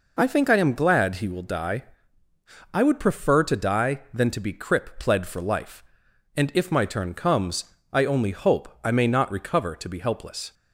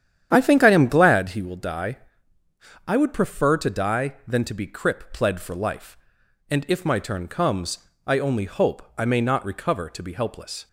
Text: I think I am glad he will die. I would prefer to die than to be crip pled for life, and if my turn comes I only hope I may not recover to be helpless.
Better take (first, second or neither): first